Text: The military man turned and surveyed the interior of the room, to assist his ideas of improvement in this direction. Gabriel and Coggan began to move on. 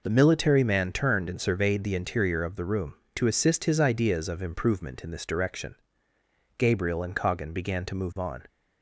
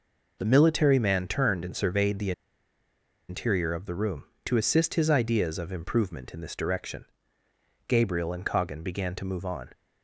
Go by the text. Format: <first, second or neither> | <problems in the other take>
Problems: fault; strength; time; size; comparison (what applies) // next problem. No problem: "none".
first | pauses between "the" and "interior"; noticeable; at 2.3 s; 0.97 s long